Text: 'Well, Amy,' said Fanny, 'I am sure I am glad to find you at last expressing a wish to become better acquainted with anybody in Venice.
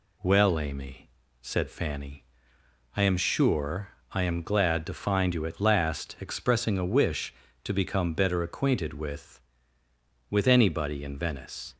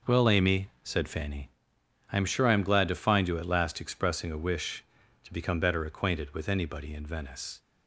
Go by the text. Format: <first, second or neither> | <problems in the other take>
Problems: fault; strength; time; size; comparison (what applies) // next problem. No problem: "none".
second | pauses between "sure" and "I"; slight; at 3.9 s; 0.20 s long // says "with" twice; at 10.3 s